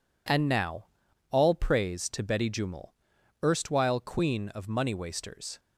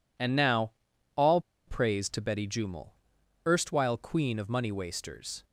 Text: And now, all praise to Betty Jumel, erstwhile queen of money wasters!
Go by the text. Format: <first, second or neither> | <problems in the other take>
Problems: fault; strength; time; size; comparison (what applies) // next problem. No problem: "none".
first | pauses between "all" and "praise"; slight; at 1.4 s; 0.26 s long